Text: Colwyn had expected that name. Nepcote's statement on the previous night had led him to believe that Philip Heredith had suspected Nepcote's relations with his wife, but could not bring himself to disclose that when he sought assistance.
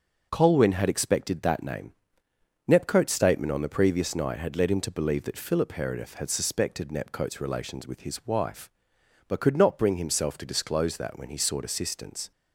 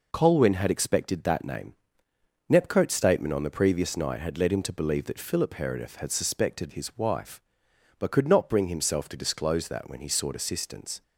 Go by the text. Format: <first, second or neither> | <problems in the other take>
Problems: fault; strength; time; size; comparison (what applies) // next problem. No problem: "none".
first | skips "Nepcote's relations with"; at 6.7 s